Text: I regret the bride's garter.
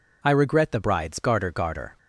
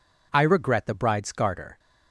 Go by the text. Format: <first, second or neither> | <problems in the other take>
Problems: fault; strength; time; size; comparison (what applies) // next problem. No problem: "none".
second | says "garter" twice; at 1.5 s